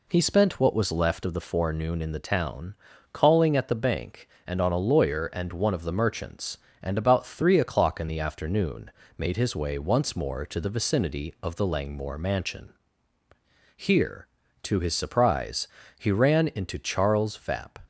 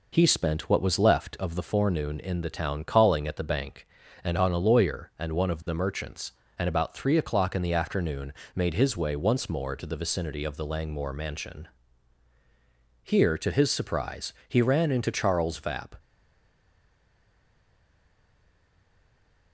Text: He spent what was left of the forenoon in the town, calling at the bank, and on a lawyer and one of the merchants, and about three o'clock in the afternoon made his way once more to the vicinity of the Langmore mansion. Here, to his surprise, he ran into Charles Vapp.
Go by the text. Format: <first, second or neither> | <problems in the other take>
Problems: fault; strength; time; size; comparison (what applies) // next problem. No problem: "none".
first | pauses between "afternoon" and "made"; slight; at 8.3 s; 0.24 s long; slight in the first // stays silent after the last word; strong; from 15.9 s on; 3.6 s long